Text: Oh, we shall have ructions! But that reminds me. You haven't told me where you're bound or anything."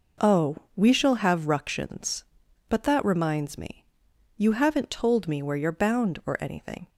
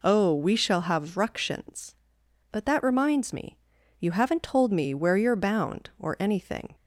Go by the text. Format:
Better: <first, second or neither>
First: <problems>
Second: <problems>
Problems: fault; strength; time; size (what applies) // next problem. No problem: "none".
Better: neither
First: none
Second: none